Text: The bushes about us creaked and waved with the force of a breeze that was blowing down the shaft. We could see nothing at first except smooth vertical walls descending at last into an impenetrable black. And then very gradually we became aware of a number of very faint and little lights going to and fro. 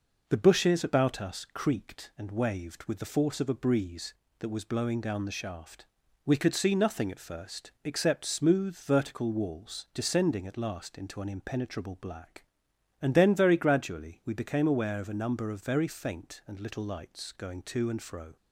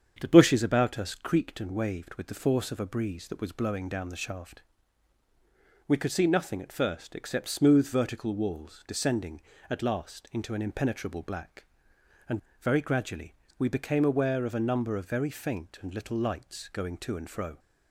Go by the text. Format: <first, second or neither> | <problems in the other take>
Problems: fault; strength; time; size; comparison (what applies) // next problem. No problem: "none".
first | starts louder than the rest; strong; until 1.2 s; 7.5 dB // skips "then"; at 12.4 s // pauses between "gradually" and "we"; slight; at 13.3 s; 0.24 s long